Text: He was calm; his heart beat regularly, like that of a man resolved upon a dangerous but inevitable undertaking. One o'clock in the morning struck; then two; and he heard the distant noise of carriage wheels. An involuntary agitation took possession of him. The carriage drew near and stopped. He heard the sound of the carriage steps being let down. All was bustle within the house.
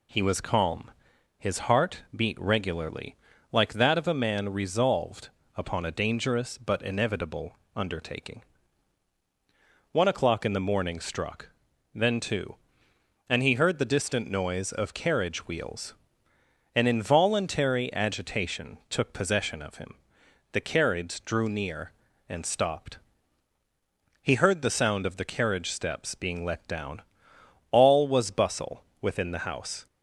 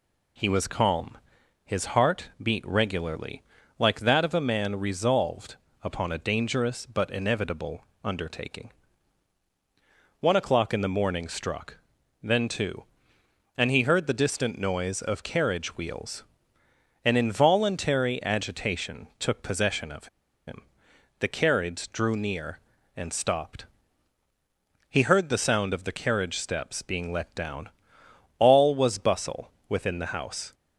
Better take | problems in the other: first | pauses between "resolved" and "upon"; slight; at 5.5 s; 0.26 s long; slight in the first // pauses between "inevitable" and "undertaking"; slight; at 7.8 s; 0.18 s long; slight in the first // pauses between "of" and "him"; at 20.0 s; 0.39 s long // pauses between "bustle" and "within"; slight; at 29.5 s; 0.16 s long; slight in the first

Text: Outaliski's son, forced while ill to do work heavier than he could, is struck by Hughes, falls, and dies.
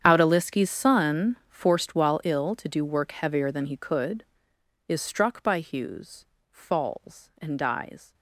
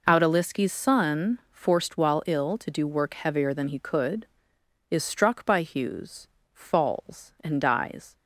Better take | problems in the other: second | gets quieter; strong; throughout; 19 dB

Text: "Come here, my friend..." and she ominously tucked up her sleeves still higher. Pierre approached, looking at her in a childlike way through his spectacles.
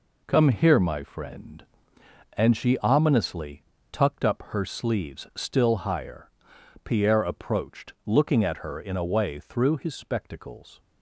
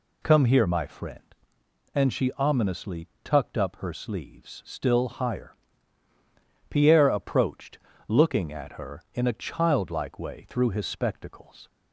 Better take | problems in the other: second | pauses between "ominously" and "tucked"; slight; at 3.6 s; 0.30 s long; slight in the second // skips "childlike"; at 9.0 s

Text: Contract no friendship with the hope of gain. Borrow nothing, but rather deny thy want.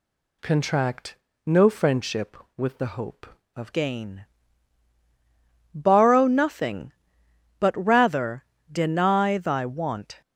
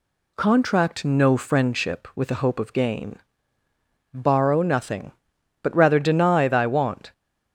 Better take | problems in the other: second | pauses between "Contract" and "no"; slight; at 1.1 s; 0.28 s long // changes voice at "gain"; from 3.7 s on; 6.5 s long // pauses between "rather" and "deny"; slight; at 8.4 s; 0.26 s long

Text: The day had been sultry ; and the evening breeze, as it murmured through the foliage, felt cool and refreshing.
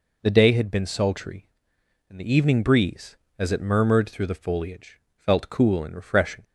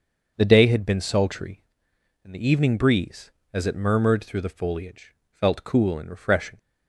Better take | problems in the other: first | starts louder than the rest; until 1.7 s; 6.5 dB

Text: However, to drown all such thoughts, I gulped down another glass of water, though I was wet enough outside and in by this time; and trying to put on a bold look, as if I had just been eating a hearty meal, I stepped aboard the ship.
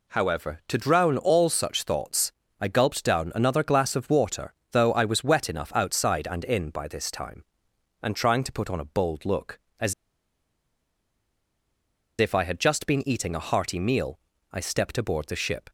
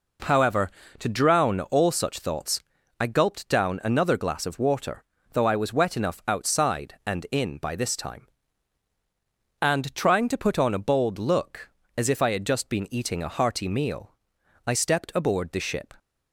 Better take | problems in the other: second | pauses between "as" and "if"; strong; at 9.9 s; 2.2 s long

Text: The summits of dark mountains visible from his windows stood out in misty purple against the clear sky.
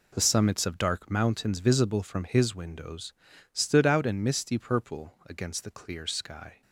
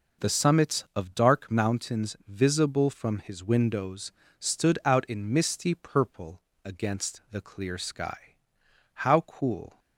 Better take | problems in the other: first | pauses between "windows" and "stood"; slight; at 4.1 s; 0.30 s long; also in the first // pauses between "purple" and "against"; slight; at 6.4 s; 0.24 s long // goes on to say "How cool"; noticeable; from 8.9 s on; 0.84 s long

